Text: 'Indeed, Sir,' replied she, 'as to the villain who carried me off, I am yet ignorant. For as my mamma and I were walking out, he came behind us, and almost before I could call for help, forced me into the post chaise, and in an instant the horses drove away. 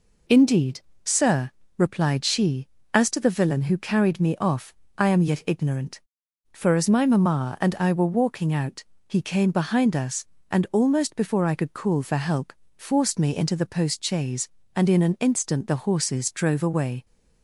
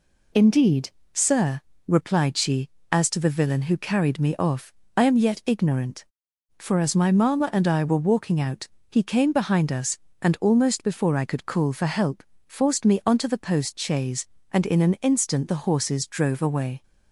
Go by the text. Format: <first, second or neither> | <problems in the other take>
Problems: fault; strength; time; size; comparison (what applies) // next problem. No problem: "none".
first | says "onto" for "into"; at 13.0 s